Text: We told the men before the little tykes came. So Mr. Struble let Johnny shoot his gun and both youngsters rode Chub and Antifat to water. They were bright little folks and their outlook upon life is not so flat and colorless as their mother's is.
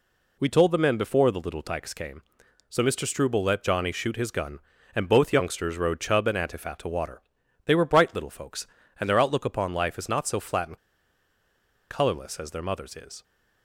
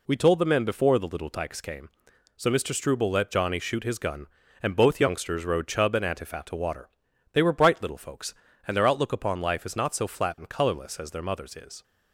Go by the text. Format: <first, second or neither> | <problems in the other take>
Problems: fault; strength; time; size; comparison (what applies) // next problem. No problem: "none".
second | pauses between "and" and "colorless"; at 10.7 s; 1.1 s long